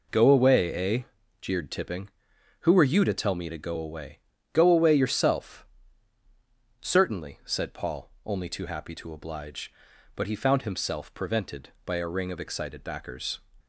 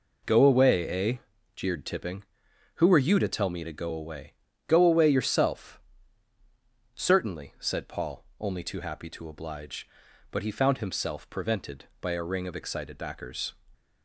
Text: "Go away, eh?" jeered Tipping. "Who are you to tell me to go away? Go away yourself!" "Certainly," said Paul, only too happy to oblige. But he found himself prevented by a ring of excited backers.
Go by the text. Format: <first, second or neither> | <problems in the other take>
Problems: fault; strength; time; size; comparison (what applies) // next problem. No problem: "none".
neither | none